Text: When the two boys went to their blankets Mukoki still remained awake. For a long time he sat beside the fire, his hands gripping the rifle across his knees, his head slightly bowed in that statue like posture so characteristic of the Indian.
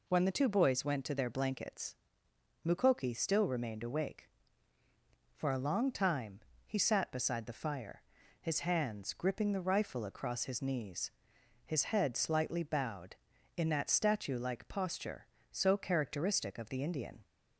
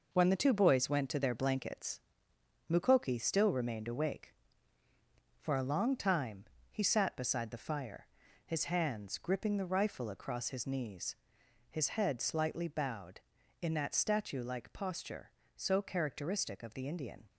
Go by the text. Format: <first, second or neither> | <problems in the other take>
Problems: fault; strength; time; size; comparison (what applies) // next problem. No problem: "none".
first | gets quieter; strong; throughout; 7 dB // pauses between "blankets" and "Mukoki"; noticeable; at 2.0 s; 0.68 s long; noticeable in the first // pauses between "time" and "he"; slight; at 6.4 s; 0.26 s long; slight in the first